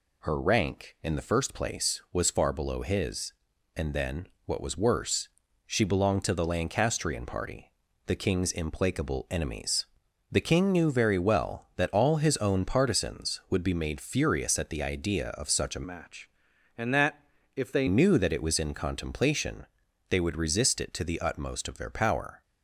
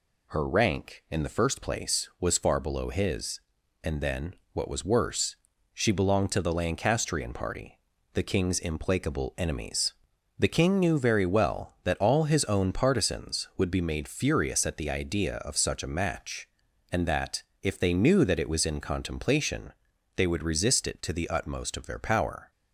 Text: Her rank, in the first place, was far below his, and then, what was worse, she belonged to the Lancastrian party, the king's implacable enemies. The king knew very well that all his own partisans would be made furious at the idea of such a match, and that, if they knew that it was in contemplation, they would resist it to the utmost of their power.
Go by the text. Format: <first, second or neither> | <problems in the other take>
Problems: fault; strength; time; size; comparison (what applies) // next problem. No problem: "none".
second | changes voice from "match" to "they"; from 15.8 to 17.8 s; 2.0 s long